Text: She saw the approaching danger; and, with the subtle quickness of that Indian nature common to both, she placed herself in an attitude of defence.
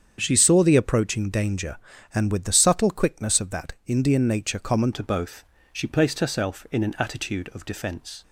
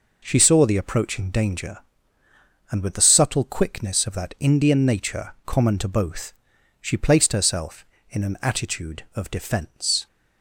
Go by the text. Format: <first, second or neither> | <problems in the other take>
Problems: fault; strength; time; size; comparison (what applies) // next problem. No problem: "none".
second | starts louder than the rest; strong; until 1.1 s; 7.5 dB // changes voice at "to"; from 4.9 s on; 3.3 s long